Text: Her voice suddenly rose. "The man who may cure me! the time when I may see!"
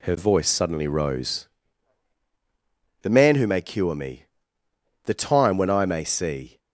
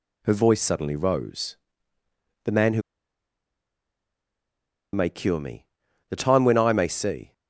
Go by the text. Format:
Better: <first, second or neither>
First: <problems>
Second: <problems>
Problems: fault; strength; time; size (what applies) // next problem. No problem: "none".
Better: first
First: none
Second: pauses between "who" and "may"; strong; at 2.8 s; 2.1 s long